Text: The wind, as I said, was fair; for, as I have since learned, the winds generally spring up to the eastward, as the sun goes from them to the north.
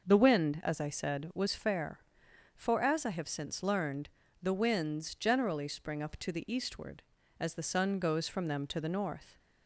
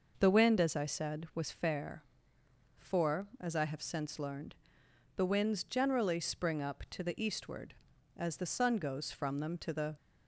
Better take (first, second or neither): first